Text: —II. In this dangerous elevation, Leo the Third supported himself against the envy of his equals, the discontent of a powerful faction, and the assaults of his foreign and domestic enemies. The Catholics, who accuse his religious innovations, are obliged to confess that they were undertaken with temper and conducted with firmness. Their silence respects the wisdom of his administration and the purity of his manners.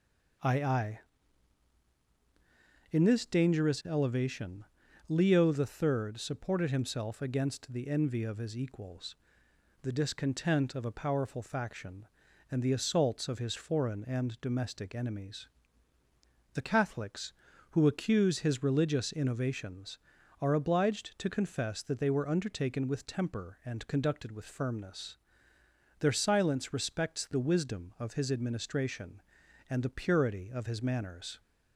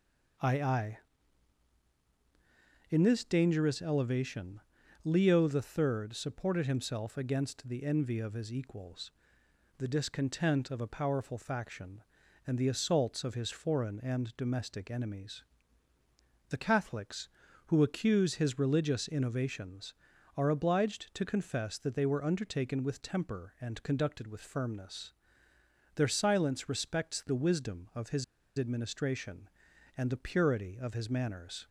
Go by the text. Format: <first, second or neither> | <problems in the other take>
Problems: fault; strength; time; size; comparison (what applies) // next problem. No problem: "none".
first | pauses between "his" and "administration"; slight; at 28.2 s; 0.34 s long